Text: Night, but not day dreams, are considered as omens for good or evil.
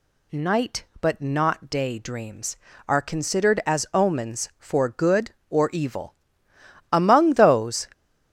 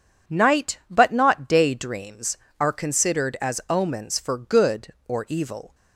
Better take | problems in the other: second | goes on to say "Among those"; noticeable; from 6.9 s on; 0.96 s long

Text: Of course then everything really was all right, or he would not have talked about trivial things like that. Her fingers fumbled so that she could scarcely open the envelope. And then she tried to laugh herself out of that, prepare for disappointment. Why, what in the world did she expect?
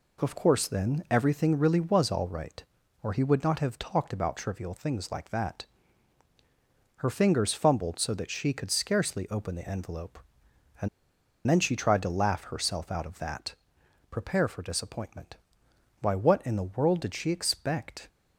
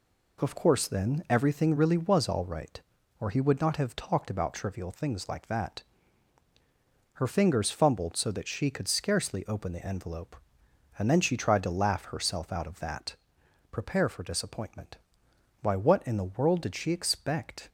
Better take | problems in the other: second | pauses between "And" and "then"; noticeable; at 10.8 s; 0.61 s long

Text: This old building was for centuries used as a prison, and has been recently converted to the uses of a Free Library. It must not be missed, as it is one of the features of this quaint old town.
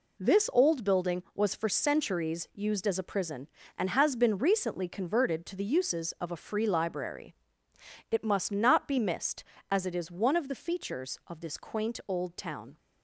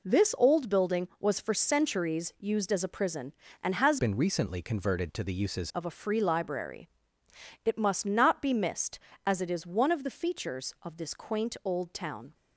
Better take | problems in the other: first | changes voice from "been" to "uses"; from 3.9 to 5.7 s; 1.8 s long

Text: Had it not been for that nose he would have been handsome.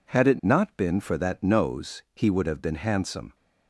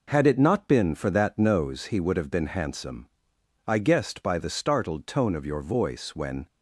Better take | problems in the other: first | goes on to say "I guessed by the startled tone of your voice when"; strong; from 3.6 s on; 2.8 s long

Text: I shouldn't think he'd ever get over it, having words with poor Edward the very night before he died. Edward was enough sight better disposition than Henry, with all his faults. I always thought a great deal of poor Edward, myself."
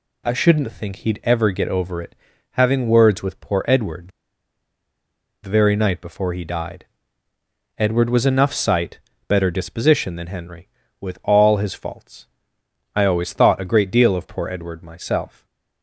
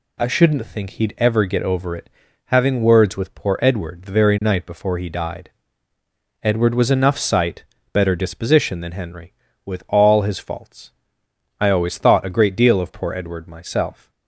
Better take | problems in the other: second | pauses between "Edward" and "the"; strong; at 4.0 s; 1.3 s long // pauses between "sight" and "better"; slight; at 8.9 s; 0.30 s long; slight in the second // stays silent after the last word; slight; from 15.2 s on; 0.6 s long

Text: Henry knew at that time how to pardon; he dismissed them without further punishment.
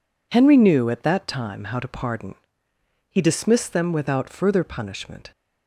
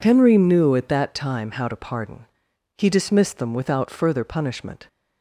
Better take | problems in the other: neither | none

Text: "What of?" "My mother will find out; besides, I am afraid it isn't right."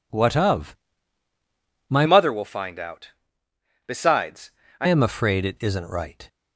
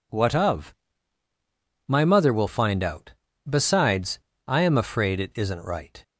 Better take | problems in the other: second | changes voice from "mother" to "I"; from 2.0 to 4.8 s; 2.8 s long

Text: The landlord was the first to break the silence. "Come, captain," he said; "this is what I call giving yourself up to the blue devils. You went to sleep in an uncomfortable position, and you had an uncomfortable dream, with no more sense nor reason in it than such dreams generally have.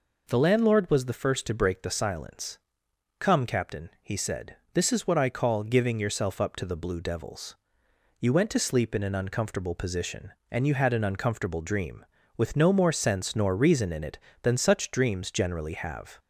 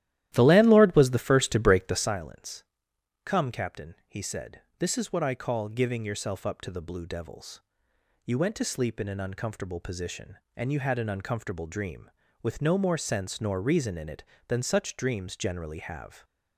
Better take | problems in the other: first | starts louder than the rest; strong; until 2.2 s; 13 dB

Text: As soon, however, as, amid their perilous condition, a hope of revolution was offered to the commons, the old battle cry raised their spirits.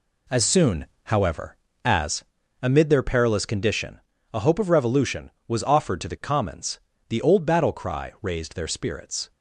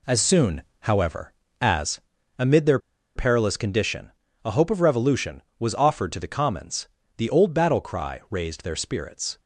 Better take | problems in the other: first | pauses between "their" and "perilous"; at 2.7 s; 0.37 s long

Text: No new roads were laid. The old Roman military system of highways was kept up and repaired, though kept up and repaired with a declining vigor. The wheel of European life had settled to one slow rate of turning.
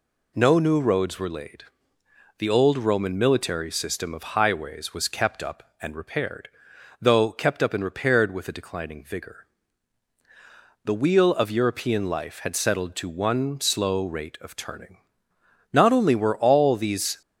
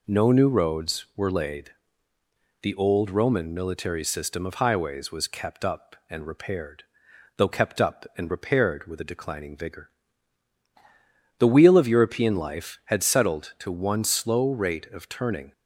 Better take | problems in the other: second | goes on to say "Not only were all these"; from 15.7 s on; 1.4 s long

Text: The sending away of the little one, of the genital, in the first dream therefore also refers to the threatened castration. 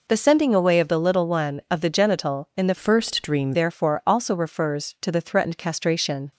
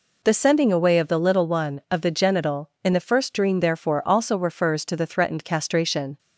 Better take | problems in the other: second | changes voice from "first" to "dream"; from 2.7 to 3.5 s; 0.8 s long

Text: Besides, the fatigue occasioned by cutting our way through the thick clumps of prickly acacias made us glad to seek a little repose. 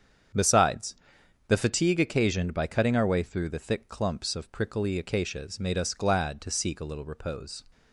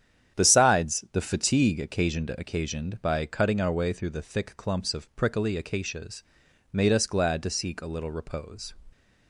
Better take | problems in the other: first | starts louder than the rest; strong; until 1.4 s; 9.5 dB; strong in the first // says "occasioned" twice; at 2.2 s // pauses between "acacias" and "made"; noticeable; at 6.2 s; 0.48 s long

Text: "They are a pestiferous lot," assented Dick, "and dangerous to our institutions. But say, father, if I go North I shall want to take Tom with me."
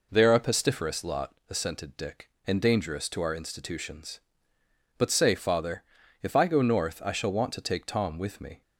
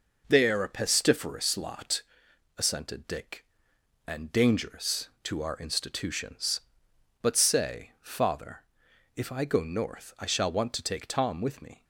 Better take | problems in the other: neither | none

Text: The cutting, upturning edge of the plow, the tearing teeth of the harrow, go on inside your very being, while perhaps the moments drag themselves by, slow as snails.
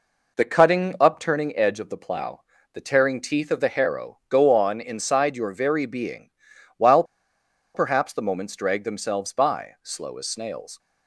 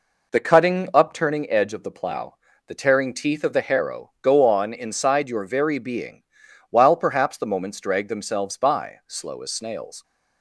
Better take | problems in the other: second | pauses between "while" and "perhaps"; noticeable; at 7.0 s; 0.70 s long

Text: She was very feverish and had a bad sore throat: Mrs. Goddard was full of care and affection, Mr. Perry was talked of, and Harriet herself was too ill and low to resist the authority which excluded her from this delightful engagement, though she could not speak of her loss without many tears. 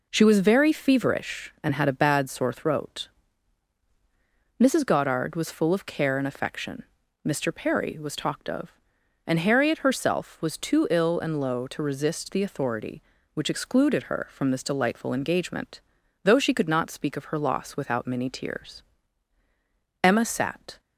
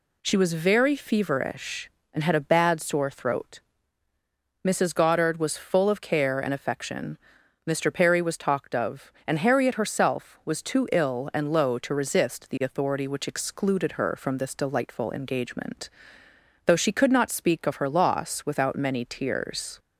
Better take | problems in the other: second | goes on to say "Emma sat"; noticeable; from 20.0 s on; 0.76 s long

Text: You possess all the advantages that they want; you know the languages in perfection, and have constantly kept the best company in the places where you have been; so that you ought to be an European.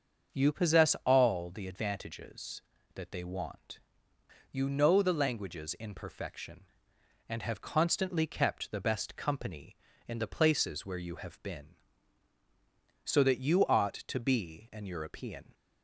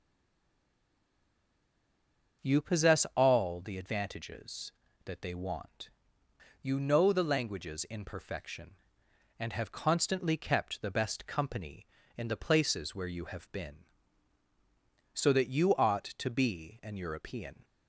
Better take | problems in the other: first | stays silent before the first word; until 2.4 s; 2.4 s long // starts louder than the rest; until 3.5 s; 6.5 dB; also in the first

